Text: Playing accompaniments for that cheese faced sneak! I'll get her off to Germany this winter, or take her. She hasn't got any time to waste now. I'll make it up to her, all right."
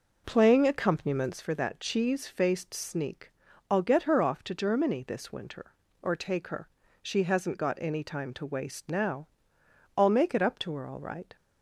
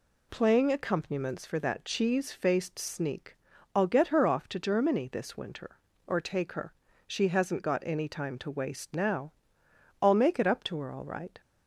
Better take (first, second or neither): second